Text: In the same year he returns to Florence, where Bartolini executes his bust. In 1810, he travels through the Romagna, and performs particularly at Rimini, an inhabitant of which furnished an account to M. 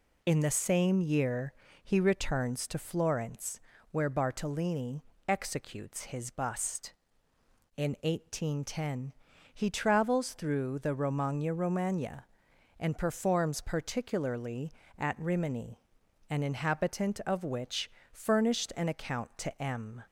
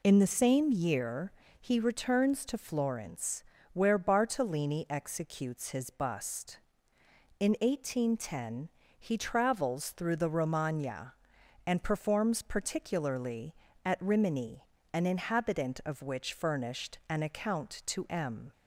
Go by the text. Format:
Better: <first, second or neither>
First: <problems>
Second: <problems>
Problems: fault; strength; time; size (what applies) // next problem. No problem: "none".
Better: second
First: pauses between "year" and "he"; slight; at 1.5 s; 0.32 s long // pauses between "Bartolini" and "executes"; slight; at 5.0 s; 0.24 s long // says "Romagna" twice; at 11.5 s // pauses between "which" and "furnished"; slight; at 17.8 s; 0.22 s long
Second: pauses between "year" and "he"; slight; at 1.3 s; 0.28 s long